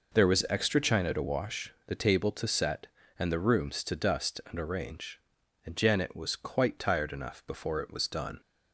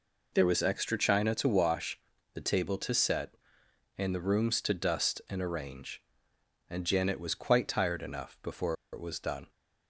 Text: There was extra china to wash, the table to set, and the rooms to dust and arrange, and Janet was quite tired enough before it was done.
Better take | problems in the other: first | pauses between "before" and "it"; slight; at 8.7 s; 0.18 s long

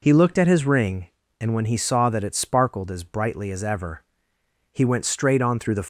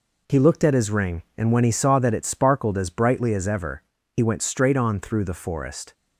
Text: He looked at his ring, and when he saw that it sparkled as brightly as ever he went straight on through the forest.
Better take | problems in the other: second | pauses between "ever" and "he"; noticeable; at 4.0 s; 0.70 s long; slight in the second // stops before "forest"; at 5.8 s

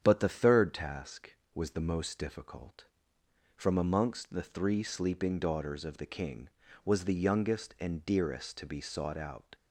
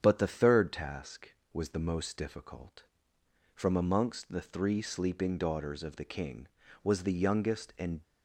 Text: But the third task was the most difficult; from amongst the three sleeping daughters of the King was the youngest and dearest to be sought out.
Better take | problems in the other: first | starts louder than the rest; strong; until 1.0 s; 8 dB; strong in the first // stops before "dearest to be sought out"; at 8.0 s

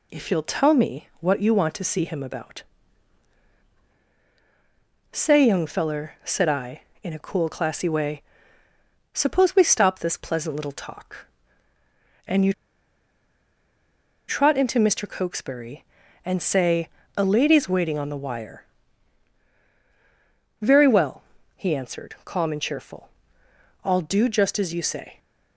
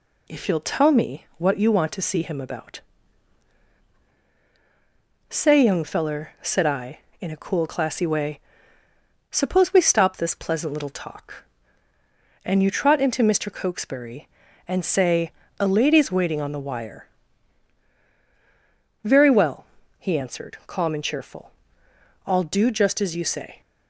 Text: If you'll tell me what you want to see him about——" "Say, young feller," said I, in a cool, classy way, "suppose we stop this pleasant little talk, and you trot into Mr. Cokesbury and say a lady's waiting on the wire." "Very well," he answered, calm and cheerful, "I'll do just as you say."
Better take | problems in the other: second | pauses between "you" and "trot"; strong; at 12.5 s; 1.7 s long // pauses between "say" and "a"; slight; at 16.8 s; 0.30 s long; slight in the second

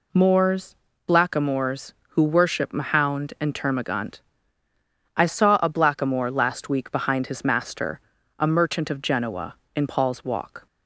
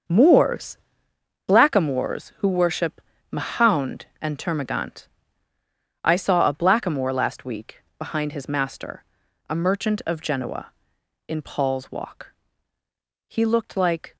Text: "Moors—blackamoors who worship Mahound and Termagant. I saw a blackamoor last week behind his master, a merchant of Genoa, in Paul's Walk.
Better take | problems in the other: first | starts louder than the rest; until 1.7 s; 6.5 dB // pauses between "worship" and "Mahound"; slight; at 2.9 s; 0.32 s long // pauses between "week" and "behind"; slight; at 7.8 s; 0.16 s long // goes on to say "He looked like"; noticeable; from 13.2 s on; 0.88 s long

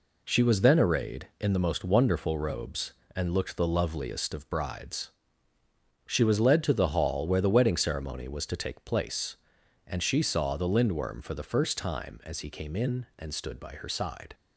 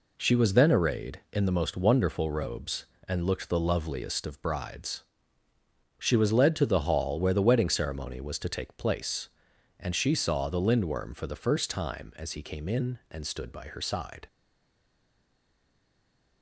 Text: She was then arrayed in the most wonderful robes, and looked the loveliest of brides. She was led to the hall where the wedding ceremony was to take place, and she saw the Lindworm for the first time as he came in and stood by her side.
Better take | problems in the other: first | stays silent after the last word; from 14.2 s on; 2.2 s long

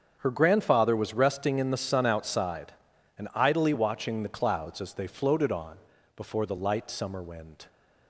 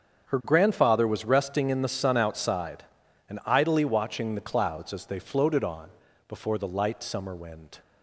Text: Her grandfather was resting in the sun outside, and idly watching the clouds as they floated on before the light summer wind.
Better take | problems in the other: neither | starts louder than the rest; the same in both // pauses between "on" and "before"; the same in both

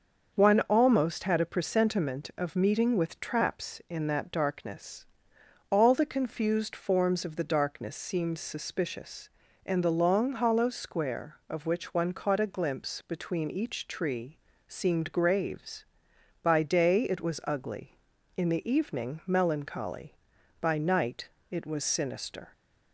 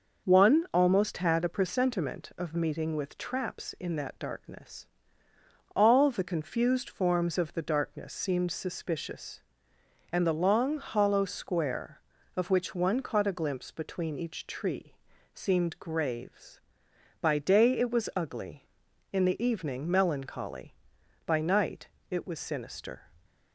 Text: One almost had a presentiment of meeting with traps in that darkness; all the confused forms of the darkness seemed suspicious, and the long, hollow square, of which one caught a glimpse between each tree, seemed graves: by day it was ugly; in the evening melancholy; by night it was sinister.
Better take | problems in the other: neither | starts louder than the rest; the same in both // pauses between "night" and "it"; slight; the same in both

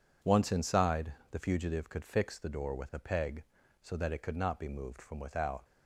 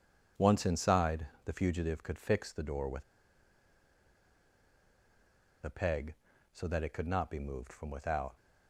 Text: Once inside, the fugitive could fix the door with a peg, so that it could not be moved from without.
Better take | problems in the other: first | pauses between "with" and "a"; strong; at 3.0 s; 2.6 s long

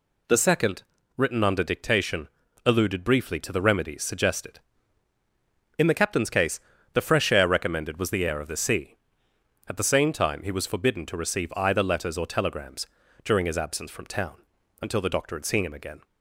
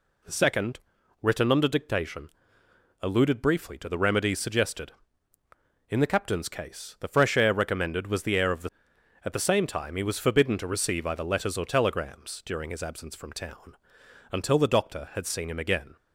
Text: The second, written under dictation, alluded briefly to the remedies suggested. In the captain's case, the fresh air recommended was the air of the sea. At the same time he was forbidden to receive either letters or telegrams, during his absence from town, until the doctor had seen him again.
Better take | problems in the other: first | skips "sea"; at 8.9 s

